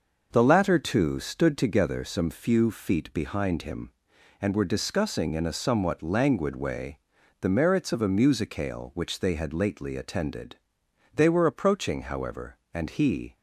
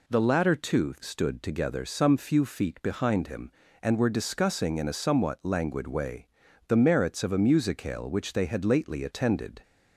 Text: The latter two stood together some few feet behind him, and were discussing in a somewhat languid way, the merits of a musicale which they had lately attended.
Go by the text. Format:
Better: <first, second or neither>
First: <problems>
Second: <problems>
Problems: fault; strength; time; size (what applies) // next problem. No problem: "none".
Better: second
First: goes on to say "They were approaching however and he"; strong; from 11.1 s on; 2.2 s long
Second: none